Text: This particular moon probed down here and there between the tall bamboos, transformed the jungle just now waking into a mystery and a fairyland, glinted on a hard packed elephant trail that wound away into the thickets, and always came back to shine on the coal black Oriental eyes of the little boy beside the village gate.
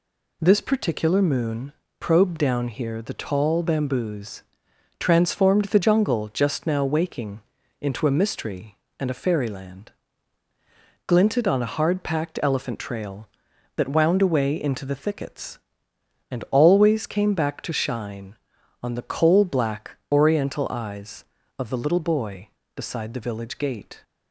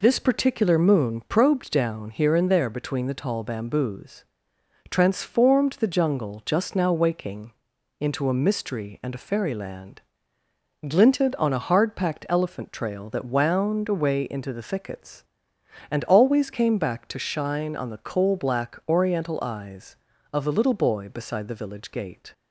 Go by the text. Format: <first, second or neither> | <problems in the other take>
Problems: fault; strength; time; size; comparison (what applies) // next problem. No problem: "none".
second | pauses between "moon" and "probed"; slight; at 1.7 s; 0.26 s long // skips "and there between"; at 3.0 s // pauses between "waking" and "into"; at 7.3 s; 0.40 s long; noticeable in the second